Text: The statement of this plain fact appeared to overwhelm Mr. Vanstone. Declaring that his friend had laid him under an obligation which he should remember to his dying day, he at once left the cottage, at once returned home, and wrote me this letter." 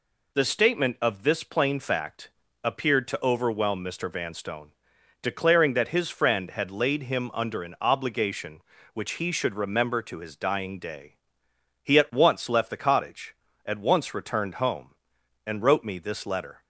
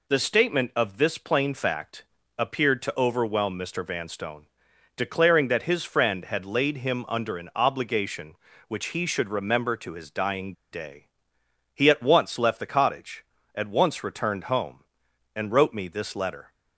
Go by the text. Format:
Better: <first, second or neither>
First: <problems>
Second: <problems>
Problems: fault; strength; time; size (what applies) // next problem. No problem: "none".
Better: first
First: pauses between "fact" and "appeared"; slight; at 2.2 s; 0.34 s long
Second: pauses between "fact" and "appeared"; slight; at 2.0 s; 0.34 s long // pauses between "dying" and "day"; slight; at 10.5 s; 0.19 s long